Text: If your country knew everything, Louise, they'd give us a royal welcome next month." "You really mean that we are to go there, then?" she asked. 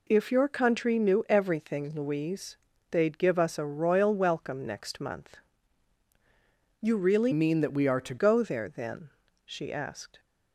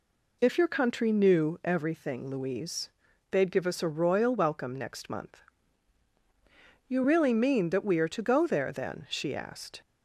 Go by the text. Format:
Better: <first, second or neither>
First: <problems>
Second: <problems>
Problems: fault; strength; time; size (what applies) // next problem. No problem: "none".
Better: second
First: changes voice from "mean" to "to"; from 7.3 to 8.1 s; 0.8 s long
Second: none